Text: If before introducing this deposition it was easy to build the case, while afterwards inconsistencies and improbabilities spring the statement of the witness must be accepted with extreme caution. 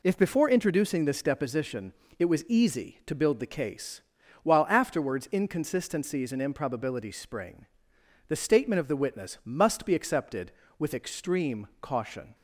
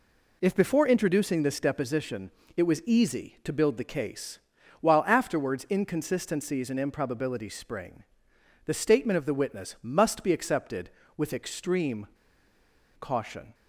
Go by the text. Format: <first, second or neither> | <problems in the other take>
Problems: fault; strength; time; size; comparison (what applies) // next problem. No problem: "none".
first | pauses between "deposition" and "it"; slight; at 2.3 s; 0.26 s long; slight in the first // pauses between "spring" and "the"; noticeable; at 8.0 s; 0.60 s long; noticeable in the first // pauses between "extreme" and "caution"; noticeable; at 12.0 s; 0.93 s long